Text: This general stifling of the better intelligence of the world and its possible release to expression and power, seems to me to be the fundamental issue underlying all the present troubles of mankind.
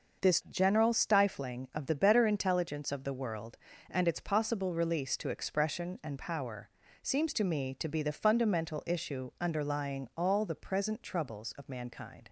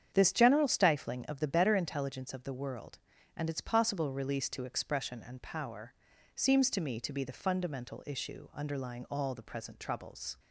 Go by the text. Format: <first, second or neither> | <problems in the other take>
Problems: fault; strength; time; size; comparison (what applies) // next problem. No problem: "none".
first | starts louder than the rest; strong; until 1.1 s; 8.5 dB // stops before "of mankind"; at 10.3 s